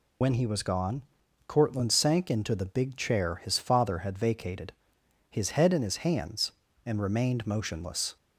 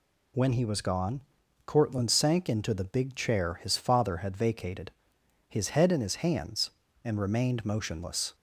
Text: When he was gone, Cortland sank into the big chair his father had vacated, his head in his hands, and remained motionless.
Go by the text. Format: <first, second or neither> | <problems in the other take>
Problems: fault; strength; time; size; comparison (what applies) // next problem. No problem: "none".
second | loses the start of "When"; at 0.2 s; 55 ms